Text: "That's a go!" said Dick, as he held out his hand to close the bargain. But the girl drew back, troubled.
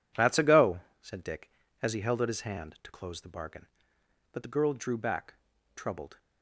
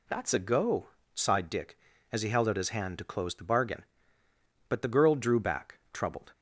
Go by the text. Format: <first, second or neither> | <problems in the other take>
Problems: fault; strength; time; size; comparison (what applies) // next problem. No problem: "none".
first | says "sighed" for "said"; at 1.1 s